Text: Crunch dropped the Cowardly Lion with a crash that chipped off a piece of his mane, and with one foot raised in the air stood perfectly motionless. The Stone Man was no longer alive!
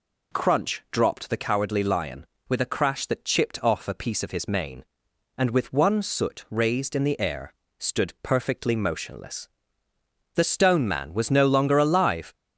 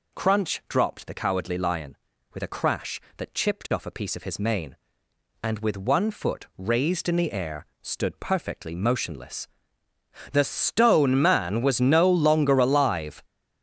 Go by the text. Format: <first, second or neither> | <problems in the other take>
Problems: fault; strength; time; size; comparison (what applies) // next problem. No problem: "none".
second | says "soot" for "foot"; at 6.0 s // pauses between "air" and "stood"; slight; at 7.5 s; 0.26 s long; slight in the second